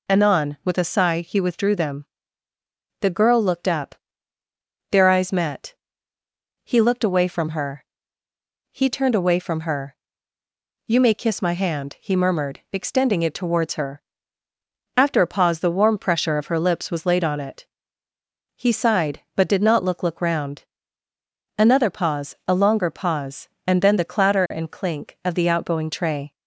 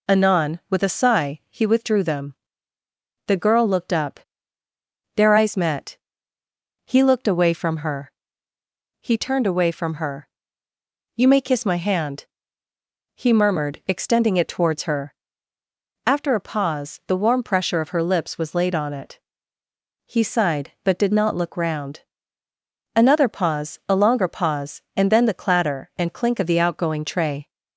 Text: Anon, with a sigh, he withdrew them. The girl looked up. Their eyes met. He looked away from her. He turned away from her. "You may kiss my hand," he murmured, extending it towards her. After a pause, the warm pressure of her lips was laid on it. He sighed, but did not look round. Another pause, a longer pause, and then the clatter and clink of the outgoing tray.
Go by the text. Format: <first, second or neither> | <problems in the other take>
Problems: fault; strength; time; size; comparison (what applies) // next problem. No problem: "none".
second | says "look" twice; at 20.0 s